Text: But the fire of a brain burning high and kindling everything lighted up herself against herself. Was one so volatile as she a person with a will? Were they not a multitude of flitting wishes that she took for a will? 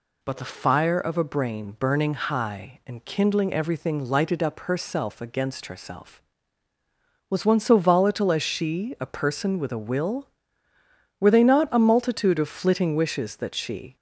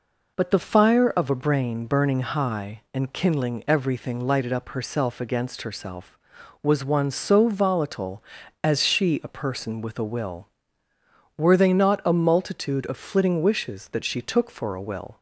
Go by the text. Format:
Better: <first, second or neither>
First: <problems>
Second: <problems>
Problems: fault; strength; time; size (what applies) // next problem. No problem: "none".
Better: second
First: stops before "took for a will"; at 13.9 s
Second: none